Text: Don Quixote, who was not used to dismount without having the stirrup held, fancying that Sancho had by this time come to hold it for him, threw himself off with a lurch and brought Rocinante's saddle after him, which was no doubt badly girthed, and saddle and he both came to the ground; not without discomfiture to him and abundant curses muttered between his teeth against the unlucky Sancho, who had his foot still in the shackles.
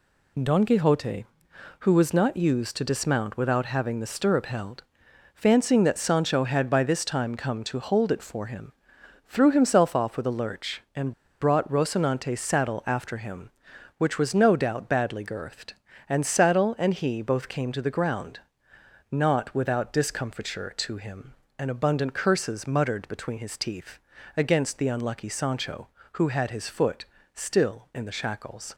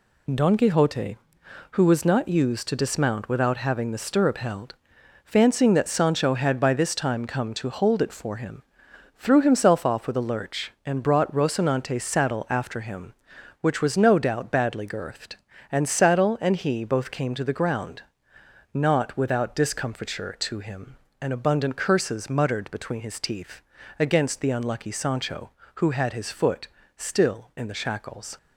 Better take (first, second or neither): second